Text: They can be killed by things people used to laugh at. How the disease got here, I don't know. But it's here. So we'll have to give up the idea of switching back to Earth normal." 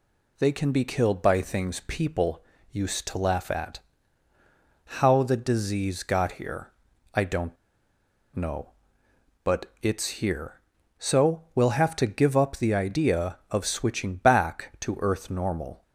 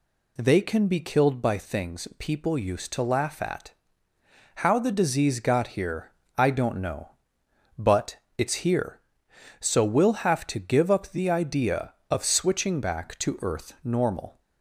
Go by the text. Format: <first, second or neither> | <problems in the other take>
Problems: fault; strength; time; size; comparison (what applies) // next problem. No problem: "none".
second | pauses between "people" and "used"; slight; at 2.4 s; 0.28 s long // pauses between "don't" and "know"; noticeable; at 7.5 s; 0.79 s long // pauses between "But" and "it's"; slight; at 9.6 s; 0.16 s long; slight in the second